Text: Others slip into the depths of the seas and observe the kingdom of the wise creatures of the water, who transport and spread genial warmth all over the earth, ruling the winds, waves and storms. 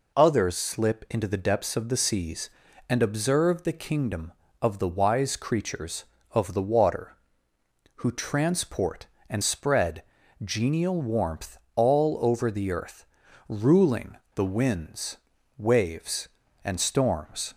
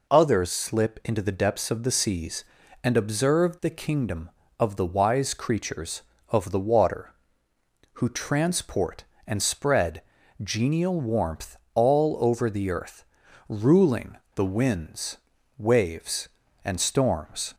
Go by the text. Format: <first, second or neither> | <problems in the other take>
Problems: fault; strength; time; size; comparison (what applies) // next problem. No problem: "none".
neither | pauses between "spread" and "genial"; the same in both // pauses between "warmth" and "all"; slight; the same in both // pauses between "ruling" and "the"; slight; the same in both